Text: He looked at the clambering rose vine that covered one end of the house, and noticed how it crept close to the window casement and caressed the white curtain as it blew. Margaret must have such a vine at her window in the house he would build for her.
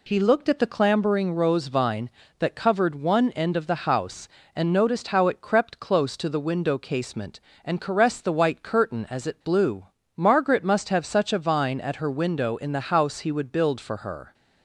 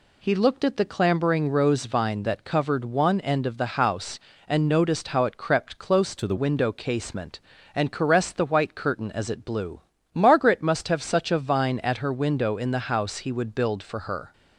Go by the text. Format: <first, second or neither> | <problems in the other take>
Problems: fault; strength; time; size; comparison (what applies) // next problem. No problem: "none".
first | changes voice from "to" to "the"; from 6.1 to 6.3 s; 0.2 s long